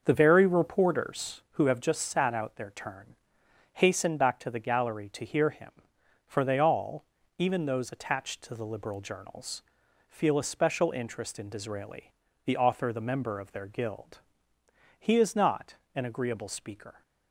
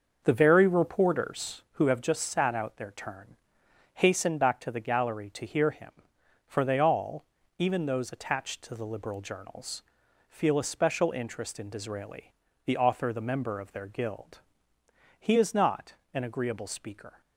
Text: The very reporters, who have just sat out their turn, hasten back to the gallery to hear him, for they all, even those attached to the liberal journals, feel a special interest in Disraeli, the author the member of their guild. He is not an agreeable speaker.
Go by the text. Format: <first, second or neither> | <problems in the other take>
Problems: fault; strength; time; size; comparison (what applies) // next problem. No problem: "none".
neither | starts louder than the rest; the same in both // pauses between "not" and "an"; slight; the same in both